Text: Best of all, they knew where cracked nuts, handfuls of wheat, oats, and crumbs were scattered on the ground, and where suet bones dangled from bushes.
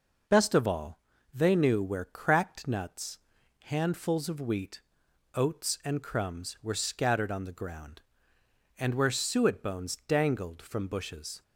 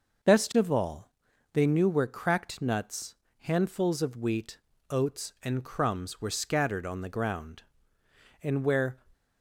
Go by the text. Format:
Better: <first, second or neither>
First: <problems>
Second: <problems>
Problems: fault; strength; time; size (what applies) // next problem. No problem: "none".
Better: first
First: none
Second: stops before "suet bones dangled from bushes"; at 9.1 s